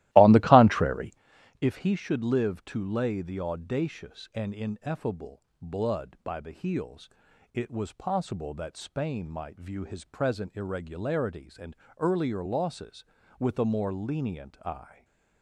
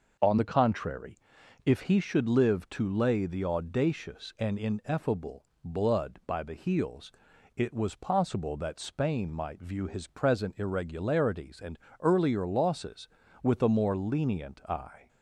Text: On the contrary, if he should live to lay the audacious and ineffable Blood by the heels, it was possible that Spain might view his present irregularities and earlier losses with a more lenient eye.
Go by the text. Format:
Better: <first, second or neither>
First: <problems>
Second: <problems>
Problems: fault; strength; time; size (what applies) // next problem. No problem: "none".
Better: second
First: starts louder than the rest; strong; until 1.2 s; 16.5 dB // pauses between "ineffable" and "Blood"; slight; at 5.4 s; 0.22 s long // pauses between "and" and "earlier"; slight; at 11.7 s; 0.24 s long // stays silent after the last word; slight; from 14.8 s on; 0.6 s long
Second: pauses between "ineffable" and "Blood"; slight; at 5.4 s; 0.22 s long // pauses between "and" and "earlier"; slight; at 11.7 s; 0.24 s long